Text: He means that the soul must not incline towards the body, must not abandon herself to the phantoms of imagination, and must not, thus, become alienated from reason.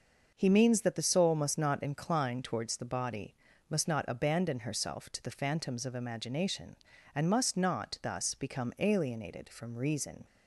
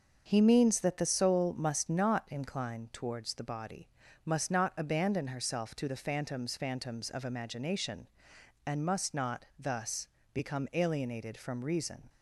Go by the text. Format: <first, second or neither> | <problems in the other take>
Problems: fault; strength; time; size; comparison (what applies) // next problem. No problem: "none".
first | starts louder than the rest; until 1.2 s; 6 dB; noticeable in the first // says "phantoms" twice; at 6.5 s